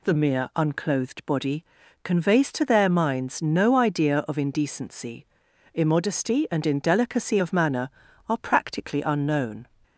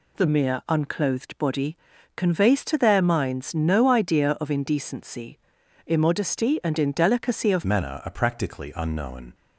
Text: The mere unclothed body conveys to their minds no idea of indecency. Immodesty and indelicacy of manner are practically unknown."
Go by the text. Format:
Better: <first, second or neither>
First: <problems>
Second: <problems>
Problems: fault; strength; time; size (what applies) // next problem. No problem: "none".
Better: first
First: pauses between "body" and "conveys"; at 1.6 s; 0.38 s long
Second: pauses between "body" and "conveys"; at 1.7 s; 0.38 s long // changes voice at "manner"; from 7.6 s on; 1.7 s long